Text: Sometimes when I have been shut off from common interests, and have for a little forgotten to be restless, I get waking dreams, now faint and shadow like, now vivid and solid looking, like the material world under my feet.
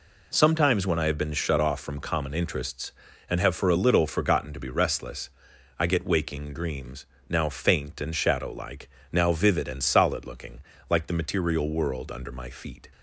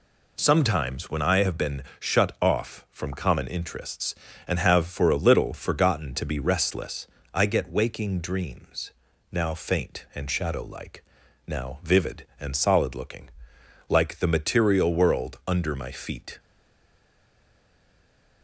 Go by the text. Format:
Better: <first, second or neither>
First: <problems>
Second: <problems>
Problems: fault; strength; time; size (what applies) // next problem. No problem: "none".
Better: first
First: none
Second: pauses between "been" and "shut"; slight; at 1.8 s; 0.18 s long // stays silent after the last word; noticeable; from 16.3 s on; 2.1 s long